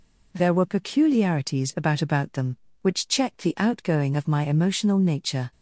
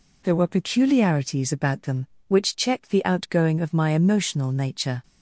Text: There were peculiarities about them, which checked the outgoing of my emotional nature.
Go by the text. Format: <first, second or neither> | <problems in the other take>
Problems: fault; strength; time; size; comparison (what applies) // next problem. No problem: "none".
second | says "about" twice; at 2.0 s